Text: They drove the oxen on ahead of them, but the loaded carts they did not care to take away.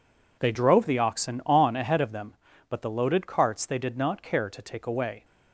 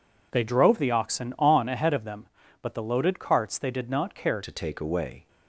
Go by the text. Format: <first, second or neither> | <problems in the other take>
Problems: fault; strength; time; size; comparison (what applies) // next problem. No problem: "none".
first | changes voice at "to"; from 4.4 s on; 0.8 s long